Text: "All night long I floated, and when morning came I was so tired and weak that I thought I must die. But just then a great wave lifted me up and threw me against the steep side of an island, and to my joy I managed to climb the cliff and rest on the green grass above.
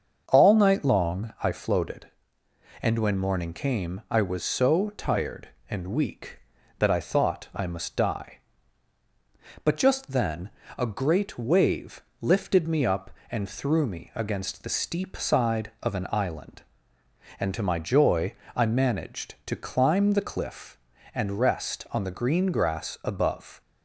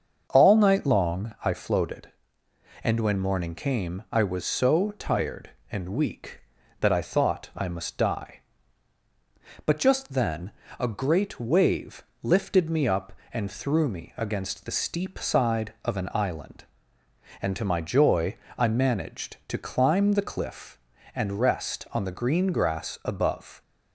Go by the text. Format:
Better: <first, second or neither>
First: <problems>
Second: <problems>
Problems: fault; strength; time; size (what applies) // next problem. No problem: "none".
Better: neither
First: starts louder than the rest; until 1.2 s; 7 dB // pauses between "then" and "a"; slight; at 10.4 s; 0.30 s long // pauses between "wave" and "lifted"; slight; at 12.0 s; 0.20 s long // pauses between "joy" and "I"; slight; at 18.3 s; 0.22 s long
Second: starts louder than the rest; until 1.3 s; 7 dB // pauses between "then" and "a"; slight; at 10.5 s; 0.30 s long // pauses between "wave" and "lifted"; slight; at 12.0 s; 0.20 s long // pauses between "joy" and "I"; slight; at 18.3 s; 0.22 s long